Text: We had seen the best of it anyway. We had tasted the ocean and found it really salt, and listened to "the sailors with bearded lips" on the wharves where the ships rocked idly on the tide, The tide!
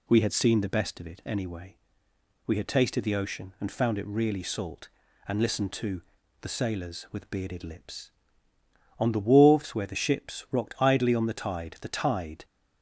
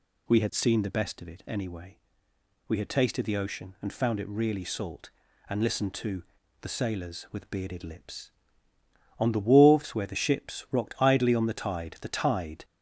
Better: first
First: pauses between "to" and "the"; at 6.0 s; 0.39 s long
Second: gets louder; slight; throughout; 3 dB // pauses between "to" and "the"; at 6.2 s; 0.38 s long

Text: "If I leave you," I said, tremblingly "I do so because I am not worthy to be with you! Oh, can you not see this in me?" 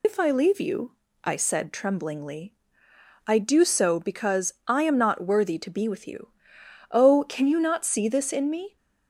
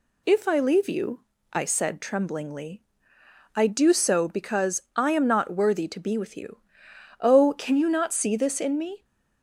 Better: second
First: loses the start of "If"; at 0.0 s; 80 ms // pauses between "tremblingly" and "I"; noticeable; at 2.5 s; 0.74 s long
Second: pauses between "tremblingly" and "I"; noticeable; at 2.8 s; 0.74 s long

